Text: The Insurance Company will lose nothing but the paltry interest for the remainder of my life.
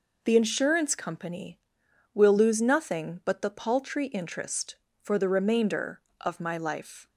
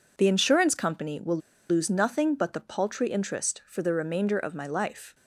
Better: first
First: none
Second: pauses between "will" and "lose"; slight; at 1.3 s; 0.31 s long

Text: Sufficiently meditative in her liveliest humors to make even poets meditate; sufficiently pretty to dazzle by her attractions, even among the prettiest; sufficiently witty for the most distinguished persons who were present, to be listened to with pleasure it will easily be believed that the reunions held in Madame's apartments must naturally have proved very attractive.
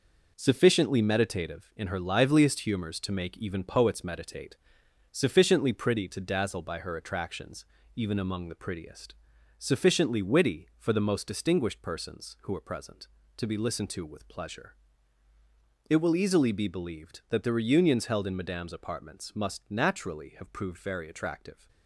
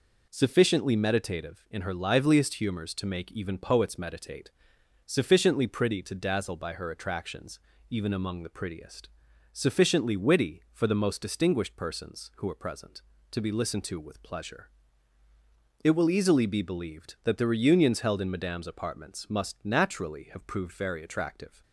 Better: second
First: gets quieter; strong; throughout; 7.5 dB // pauses between "pleasure" and "it"; at 14.7 s; 1.1 s long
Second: pauses between "pleasure" and "it"; at 14.6 s; 1.1 s long

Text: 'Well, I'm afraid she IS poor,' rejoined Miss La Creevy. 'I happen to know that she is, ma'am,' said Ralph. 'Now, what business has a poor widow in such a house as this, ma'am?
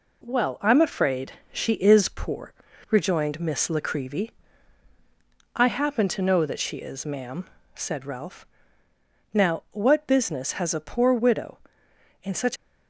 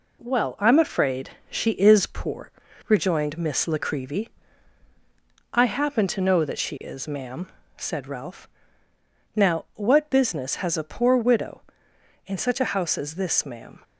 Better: second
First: pauses between "afraid" and "she"; slight; at 1.3 s; 0.18 s long // stops before "a house as this ma'am"; at 12.5 s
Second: pauses between "afraid" and "she"; slight; at 1.3 s; 0.18 s long

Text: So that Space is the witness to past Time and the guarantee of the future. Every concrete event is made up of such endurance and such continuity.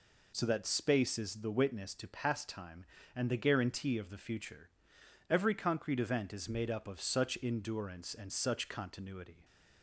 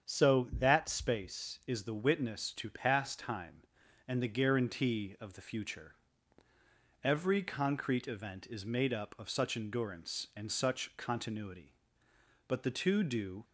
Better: first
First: none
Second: starts louder than the rest; strong; until 1.1 s; 7.5 dB // goes on to say "But the two do"; noticeable; from 12.4 s on; 0.96 s long

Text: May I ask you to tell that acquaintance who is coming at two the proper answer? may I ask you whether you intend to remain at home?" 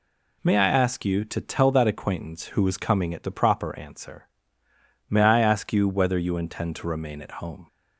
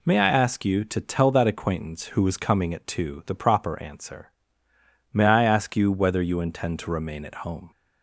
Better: second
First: skips "two"; at 3.2 s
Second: none

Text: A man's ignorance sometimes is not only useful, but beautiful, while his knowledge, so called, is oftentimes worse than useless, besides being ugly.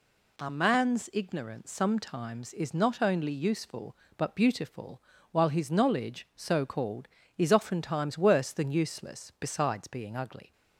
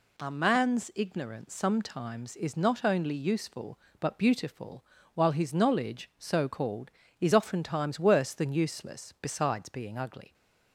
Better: neither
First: none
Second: none

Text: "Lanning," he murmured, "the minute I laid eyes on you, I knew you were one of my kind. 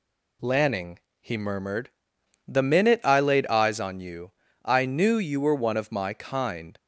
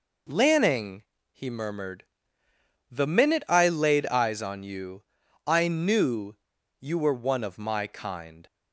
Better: first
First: none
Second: pauses between "knew" and "you"; noticeable; at 6.3 s; 0.46 s long

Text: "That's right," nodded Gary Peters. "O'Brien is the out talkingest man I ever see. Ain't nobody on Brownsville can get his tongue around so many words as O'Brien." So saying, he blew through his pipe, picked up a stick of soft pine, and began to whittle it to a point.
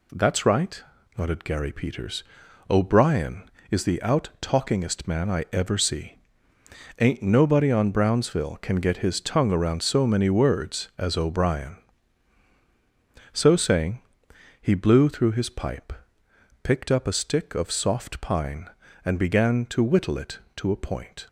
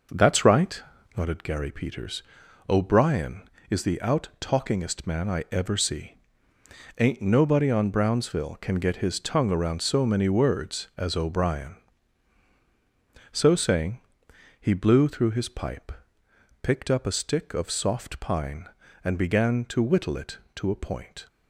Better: first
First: none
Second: starts louder than the rest; noticeable; until 1.2 s; 6 dB

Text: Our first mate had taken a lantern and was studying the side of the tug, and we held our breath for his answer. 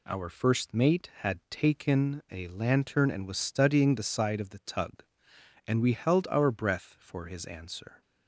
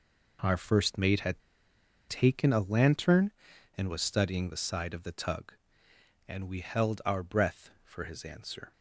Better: first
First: none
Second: pauses between "had" and "taken"; noticeable; at 1.4 s; 0.69 s long

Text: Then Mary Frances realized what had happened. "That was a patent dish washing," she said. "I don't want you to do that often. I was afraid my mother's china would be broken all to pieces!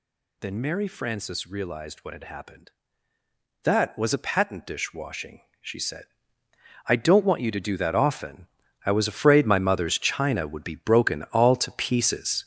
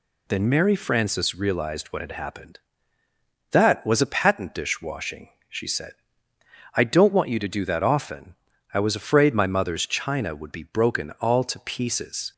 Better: second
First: gets louder; strong; throughout; 7.5 dB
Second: none

